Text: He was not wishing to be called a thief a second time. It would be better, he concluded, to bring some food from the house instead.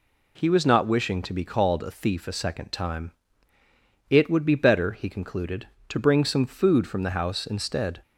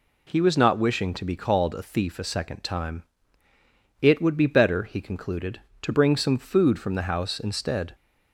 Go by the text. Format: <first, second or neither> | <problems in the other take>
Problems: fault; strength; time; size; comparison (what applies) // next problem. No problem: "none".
neither | none